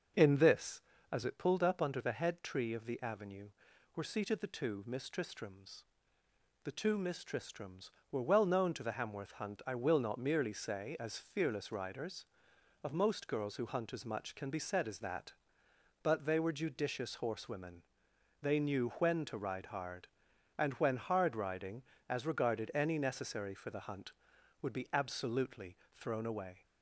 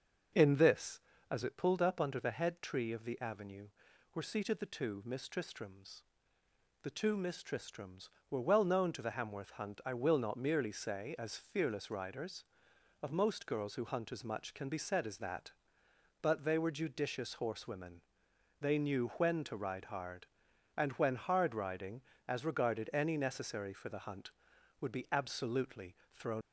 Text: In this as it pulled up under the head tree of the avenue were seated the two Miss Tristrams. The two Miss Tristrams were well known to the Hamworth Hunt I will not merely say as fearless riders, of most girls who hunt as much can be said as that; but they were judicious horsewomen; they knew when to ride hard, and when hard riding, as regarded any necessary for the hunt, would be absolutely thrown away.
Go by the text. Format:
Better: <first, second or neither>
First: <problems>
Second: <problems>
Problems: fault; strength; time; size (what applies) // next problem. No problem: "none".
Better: first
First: pauses between "absolutely" and "thrown"; slight; at 25.7 s; 0.18 s long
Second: pauses between "absolutely" and "thrown"; slight; at 25.9 s; 0.18 s long // stops before "away"; at 26.4 s